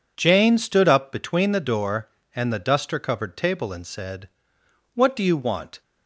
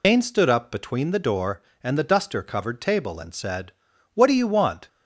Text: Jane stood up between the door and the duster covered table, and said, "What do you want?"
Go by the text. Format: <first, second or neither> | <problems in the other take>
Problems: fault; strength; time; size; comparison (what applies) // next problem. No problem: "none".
first | loses the start of "Jane"; at 0.0 s; 130 ms